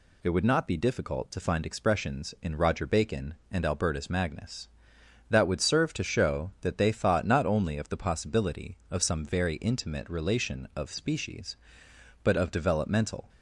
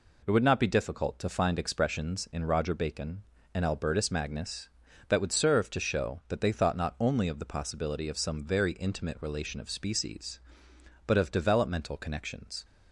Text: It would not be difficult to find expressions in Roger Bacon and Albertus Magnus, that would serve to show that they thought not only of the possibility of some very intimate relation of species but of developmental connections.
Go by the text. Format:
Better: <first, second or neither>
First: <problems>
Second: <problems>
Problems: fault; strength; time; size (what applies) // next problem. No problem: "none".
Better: second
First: stops before "connections"; at 13.2 s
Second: none